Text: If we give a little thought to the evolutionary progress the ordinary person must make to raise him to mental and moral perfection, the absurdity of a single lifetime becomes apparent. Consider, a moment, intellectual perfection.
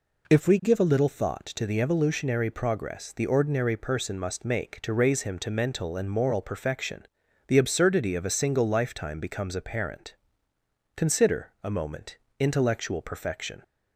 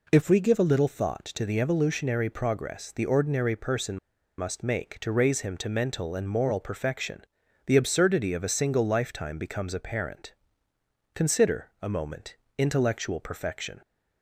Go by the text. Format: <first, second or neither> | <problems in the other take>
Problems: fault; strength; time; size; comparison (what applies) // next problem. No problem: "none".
first | pauses between "person" and "must"; at 3.9 s; 0.40 s long